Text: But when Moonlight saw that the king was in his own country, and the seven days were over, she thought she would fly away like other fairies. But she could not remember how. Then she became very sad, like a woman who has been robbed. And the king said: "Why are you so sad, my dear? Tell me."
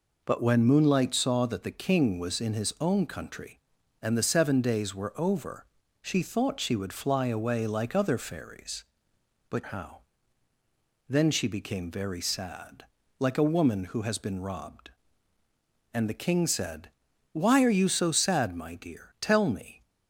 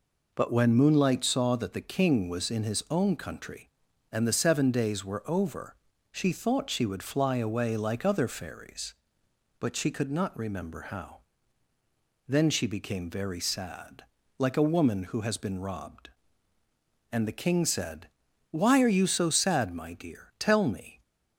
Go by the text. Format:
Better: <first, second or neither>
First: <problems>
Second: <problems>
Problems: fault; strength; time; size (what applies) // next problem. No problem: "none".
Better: second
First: skips "she could not remember"; at 9.6 s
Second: none